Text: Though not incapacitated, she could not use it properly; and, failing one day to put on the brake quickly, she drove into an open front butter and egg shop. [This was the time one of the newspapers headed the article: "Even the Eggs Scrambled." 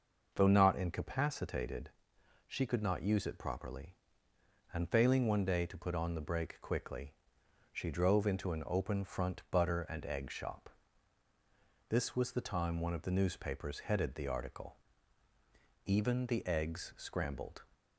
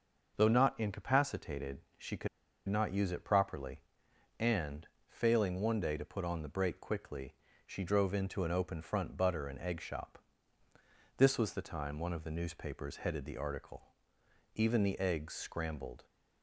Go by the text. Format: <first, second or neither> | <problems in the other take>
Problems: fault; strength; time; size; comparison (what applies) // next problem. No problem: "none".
first | starts louder than the rest; until 1.4 s; 6.5 dB // pauses between "could" and "not"; at 2.2 s; 0.41 s long